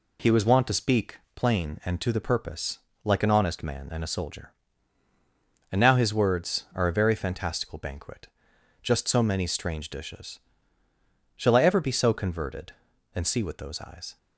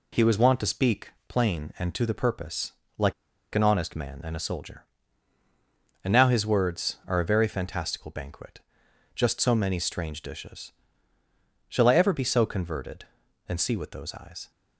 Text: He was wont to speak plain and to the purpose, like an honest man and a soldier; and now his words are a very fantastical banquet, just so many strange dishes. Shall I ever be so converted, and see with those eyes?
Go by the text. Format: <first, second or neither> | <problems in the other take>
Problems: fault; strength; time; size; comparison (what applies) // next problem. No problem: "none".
first | pauses between "speak" and "plain"; slight; at 1.0 s; 0.18 s long; slight in the first // pauses between "like" and "an"; at 3.1 s; 0.41 s long